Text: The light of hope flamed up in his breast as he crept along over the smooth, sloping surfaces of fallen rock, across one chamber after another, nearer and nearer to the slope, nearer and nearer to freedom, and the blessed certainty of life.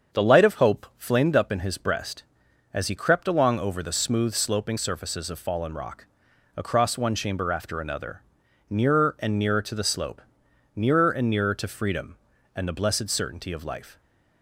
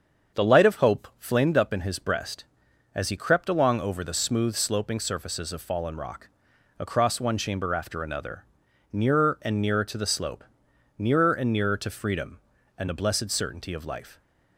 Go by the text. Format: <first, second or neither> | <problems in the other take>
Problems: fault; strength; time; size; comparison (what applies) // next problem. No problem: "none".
neither | starts louder than the rest; strong; the same in both